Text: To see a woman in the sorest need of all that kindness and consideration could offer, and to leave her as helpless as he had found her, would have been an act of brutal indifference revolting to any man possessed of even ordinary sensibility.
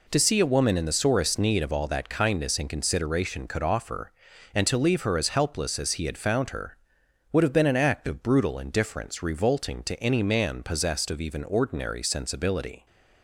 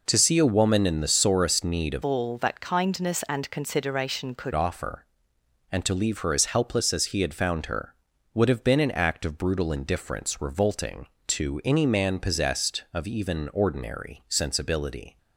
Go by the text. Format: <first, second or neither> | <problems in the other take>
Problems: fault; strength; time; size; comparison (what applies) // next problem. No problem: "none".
first | changes voice from "all" to "could"; from 2.0 to 4.5 s; 2.5 s long